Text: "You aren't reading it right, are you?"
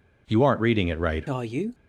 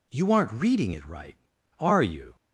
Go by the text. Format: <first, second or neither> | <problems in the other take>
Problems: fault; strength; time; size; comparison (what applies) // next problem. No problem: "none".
second | changes voice at "are"; from 1.2 s on; 0.5 s long